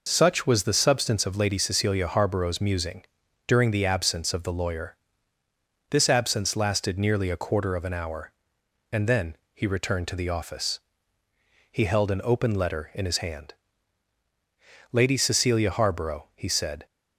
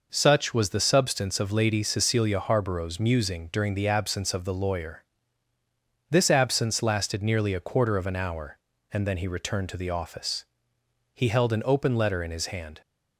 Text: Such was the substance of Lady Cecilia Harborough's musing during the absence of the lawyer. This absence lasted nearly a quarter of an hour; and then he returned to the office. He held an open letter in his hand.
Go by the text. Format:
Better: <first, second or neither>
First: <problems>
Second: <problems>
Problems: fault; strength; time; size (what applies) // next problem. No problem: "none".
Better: second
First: pauses between "musing" and "during"; at 3.0 s; 0.42 s long // pauses between "then" and "he"; slight; at 9.3 s; 0.18 s long // goes on to say "Lady Cecilia Harborough he said"; strong; from 14.9 s on; 1.9 s long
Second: none